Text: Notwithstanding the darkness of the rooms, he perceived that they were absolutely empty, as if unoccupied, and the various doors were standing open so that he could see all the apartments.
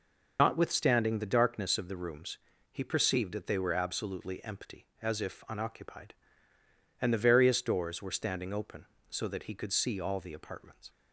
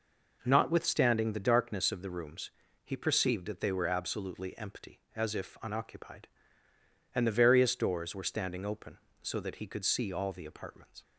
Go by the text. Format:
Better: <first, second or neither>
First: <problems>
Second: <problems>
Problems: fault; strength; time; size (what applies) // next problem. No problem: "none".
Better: second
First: loses the start of "Notwithstanding"; at 0.3 s; 130 ms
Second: none